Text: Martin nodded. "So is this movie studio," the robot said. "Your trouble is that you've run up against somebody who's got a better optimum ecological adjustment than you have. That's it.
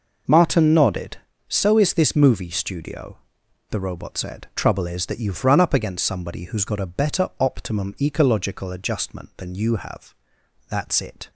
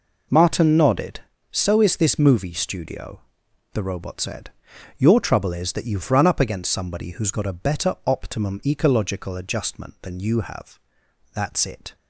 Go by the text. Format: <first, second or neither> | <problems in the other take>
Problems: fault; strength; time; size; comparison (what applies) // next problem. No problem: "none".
second | skips "Your"; at 4.5 s